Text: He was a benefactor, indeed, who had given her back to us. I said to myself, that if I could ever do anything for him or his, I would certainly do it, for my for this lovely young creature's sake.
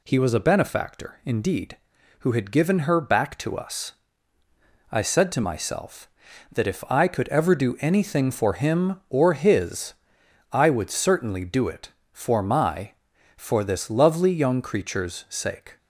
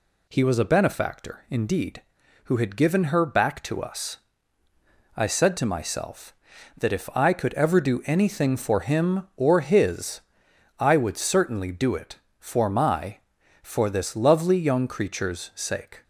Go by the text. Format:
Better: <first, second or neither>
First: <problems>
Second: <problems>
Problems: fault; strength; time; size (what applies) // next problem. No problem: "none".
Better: neither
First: none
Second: none